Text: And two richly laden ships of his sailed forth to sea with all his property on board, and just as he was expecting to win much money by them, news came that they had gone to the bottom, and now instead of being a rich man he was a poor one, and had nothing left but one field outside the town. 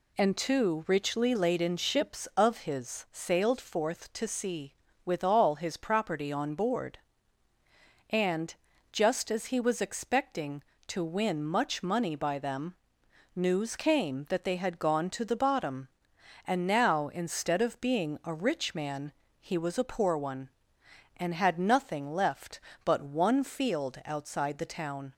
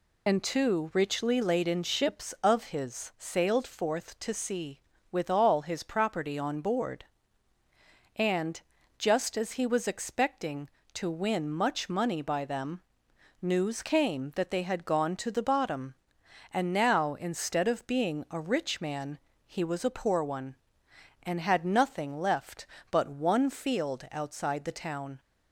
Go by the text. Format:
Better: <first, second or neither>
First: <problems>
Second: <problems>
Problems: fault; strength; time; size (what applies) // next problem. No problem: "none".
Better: first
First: pauses between "and" and "just"; at 8.5 s; 0.38 s long // pauses between "man" and "he"; slight; at 19.1 s; 0.26 s long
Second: loses the start of "And"; at 0.2 s; 40 ms // pauses between "and" and "just"; at 8.5 s; 0.38 s long // pauses between "man" and "he"; slight; at 19.1 s; 0.26 s long